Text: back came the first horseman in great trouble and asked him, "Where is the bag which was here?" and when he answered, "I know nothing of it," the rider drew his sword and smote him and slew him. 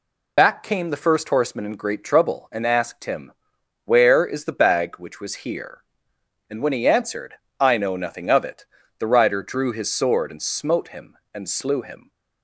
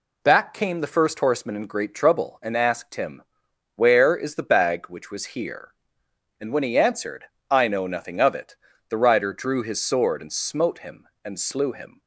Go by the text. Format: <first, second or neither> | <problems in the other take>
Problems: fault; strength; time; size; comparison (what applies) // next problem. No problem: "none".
second | loses the start of "back"; at 0.3 s; 55 ms